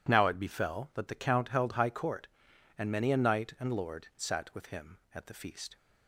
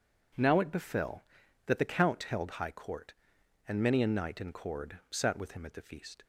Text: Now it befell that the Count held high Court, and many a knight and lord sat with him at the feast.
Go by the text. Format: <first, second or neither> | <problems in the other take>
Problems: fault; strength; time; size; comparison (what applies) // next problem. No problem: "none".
first | says "cord" for "lord"; at 4.5 s